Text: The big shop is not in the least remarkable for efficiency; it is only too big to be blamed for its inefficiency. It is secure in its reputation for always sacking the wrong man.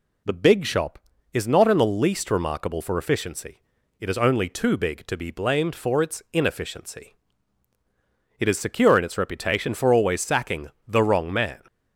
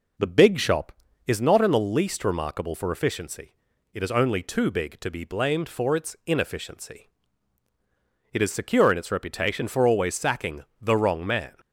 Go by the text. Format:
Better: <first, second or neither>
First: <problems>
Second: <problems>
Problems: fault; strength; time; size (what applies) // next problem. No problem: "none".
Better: first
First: pauses between "sacking" and "the"; slight; at 10.6 s; 0.18 s long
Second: starts louder than the rest; noticeable; until 1.5 s; 4.5 dB // pauses between "sacking" and "the"; slight; at 10.6 s; 0.18 s long